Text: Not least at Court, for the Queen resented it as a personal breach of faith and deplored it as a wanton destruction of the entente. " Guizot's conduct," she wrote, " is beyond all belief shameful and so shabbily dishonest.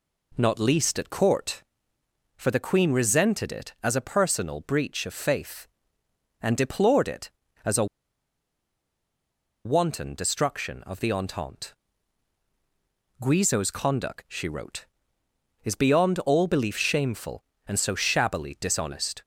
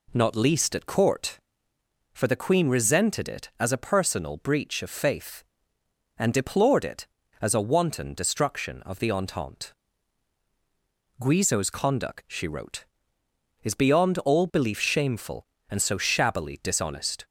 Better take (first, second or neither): second